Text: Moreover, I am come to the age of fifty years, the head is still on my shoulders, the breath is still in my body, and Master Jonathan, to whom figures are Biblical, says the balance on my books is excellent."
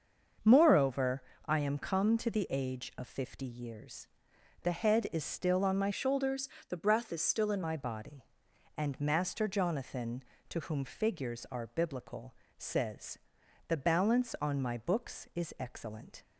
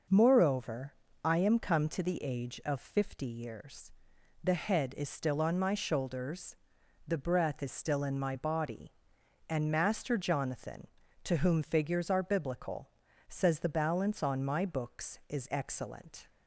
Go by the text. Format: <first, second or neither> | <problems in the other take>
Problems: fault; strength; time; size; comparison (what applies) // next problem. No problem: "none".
second | starts louder than the rest; until 1.6 s; 6.5 dB // changes voice from "shoulders" to "in"; from 5.9 to 7.6 s; 1.7 s long // pauses between "says" and "the"; noticeable; at 13.1 s; 0.50 s long